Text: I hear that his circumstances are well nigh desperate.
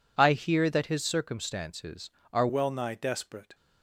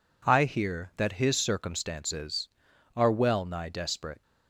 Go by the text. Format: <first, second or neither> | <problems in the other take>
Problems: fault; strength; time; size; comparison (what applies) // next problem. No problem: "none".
second | changes voice at "well"; from 2.4 s on; 1.1 s long